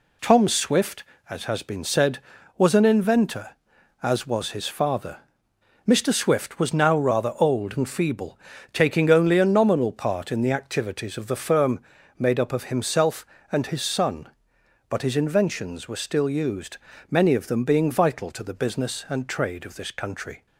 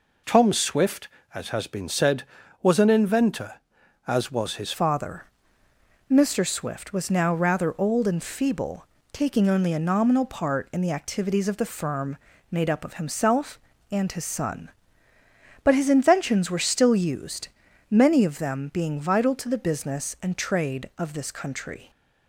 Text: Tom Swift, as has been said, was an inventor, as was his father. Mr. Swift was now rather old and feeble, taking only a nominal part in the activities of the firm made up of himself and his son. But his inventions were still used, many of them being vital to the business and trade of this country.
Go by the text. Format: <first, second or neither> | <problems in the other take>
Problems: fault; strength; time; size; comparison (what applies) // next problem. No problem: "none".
first | changes voice at "father"; from 4.7 s on; 17.1 s long // pauses between "firm" and "made"; slight; at 12.1 s; 0.34 s long; also in the first